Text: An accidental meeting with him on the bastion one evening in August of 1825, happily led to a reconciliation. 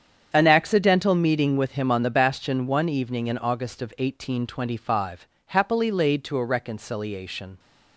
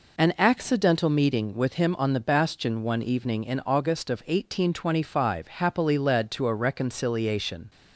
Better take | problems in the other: second | starts louder than the rest; strong; until 1.3 s; 8 dB // says "laid" for "led"; at 5.9 s

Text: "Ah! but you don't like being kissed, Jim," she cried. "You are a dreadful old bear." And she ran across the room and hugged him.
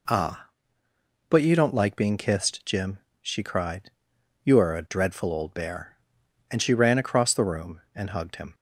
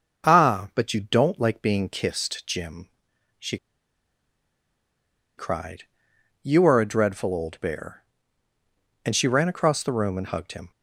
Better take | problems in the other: first | starts louder than the rest; until 1.3 s; 6 dB // pauses between "she" and "cried"; strong; at 3.5 s; 1.8 s long

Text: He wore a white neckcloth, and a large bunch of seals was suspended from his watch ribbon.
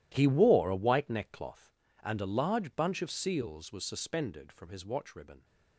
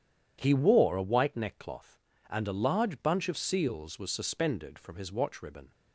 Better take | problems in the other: second | gets quieter; strong; throughout; 17 dB

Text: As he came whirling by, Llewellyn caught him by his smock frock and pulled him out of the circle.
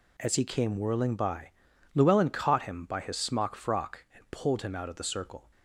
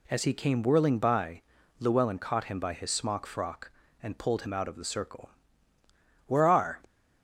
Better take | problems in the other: first | goes on to say "Where are"; from 6.2 s on; 0.54 s long

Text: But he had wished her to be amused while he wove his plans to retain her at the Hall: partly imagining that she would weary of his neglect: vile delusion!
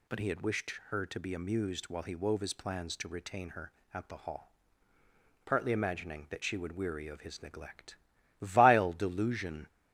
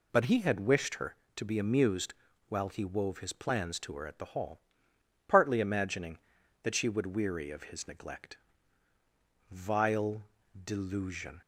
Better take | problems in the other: first | pauses between "amused" and "while"; slight; at 2.1 s; 0.36 s long // skips "retain"; at 3.9 s // pauses between "vile" and "delusion"; at 10.2 s; 0.38 s long

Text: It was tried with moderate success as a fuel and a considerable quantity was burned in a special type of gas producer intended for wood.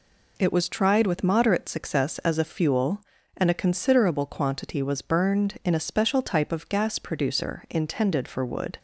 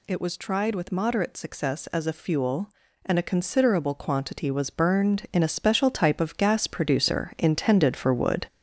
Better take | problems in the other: first | gets louder; noticeable; throughout; 6 dB

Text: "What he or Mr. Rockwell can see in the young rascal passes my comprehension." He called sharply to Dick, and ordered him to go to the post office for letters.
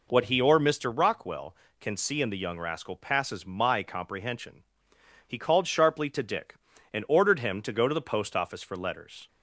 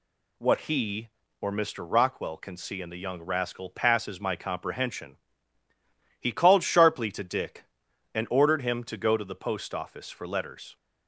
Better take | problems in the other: second | starts louder than the rest; noticeable; until 1.2 s; 4.5 dB

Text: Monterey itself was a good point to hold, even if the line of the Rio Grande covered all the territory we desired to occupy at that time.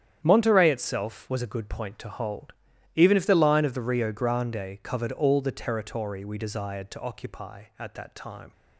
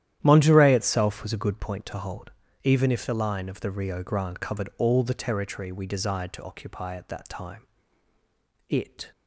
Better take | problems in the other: first | starts louder than the rest; strong; until 1.2 s; 11.5 dB; strong in the first // goes on to say "It"; slight; from 8.6 s on; 0.42 s long

